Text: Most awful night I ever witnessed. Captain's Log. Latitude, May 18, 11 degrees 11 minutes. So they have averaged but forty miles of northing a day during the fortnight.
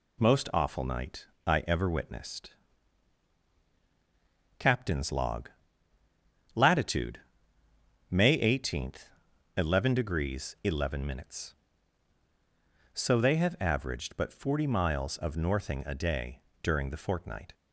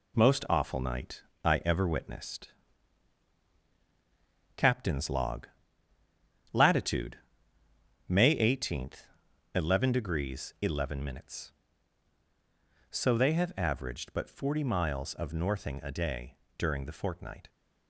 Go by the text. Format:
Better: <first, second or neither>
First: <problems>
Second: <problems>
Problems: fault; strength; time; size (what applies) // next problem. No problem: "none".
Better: first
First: pauses between "night" and "I"; slight; at 1.2 s; 0.18 s long // pauses between "day" and "during"; slight; at 16.4 s; 0.22 s long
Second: gets quieter; noticeable; throughout; 5 dB // pauses between "night" and "I"; slight; at 1.2 s; 0.20 s long // pauses between "day" and "during"; slight; at 16.3 s; 0.22 s long